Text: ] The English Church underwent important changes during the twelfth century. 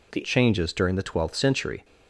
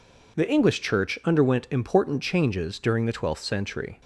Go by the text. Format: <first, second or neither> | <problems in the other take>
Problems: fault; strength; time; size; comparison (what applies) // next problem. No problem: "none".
second | skips "English Church underwent important"; at 0.2 s